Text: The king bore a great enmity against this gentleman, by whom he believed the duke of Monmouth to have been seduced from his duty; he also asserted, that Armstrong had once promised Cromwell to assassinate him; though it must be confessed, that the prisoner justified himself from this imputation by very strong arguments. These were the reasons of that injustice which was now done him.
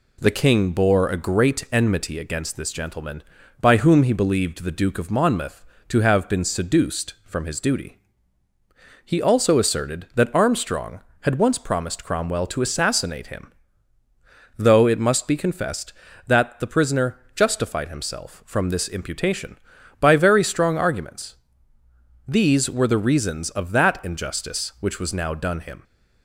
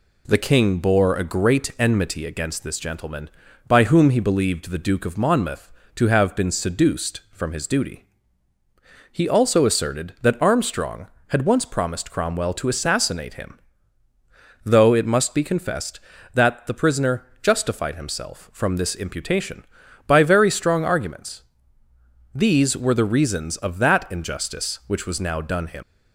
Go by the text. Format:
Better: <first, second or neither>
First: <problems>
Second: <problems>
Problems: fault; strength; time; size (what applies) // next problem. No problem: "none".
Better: first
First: pauses between "prisoner" and "justified"; slight; at 17.1 s; 0.16 s long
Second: pauses between "prisoner" and "justified"; slight; at 17.2 s; 0.16 s long // leaves "him" unfinished; at 25.8 s; 70 ms